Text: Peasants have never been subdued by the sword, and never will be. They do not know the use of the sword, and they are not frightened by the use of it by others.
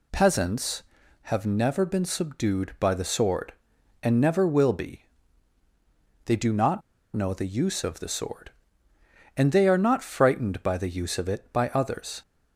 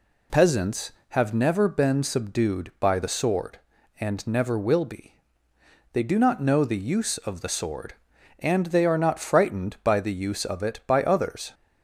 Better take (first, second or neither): second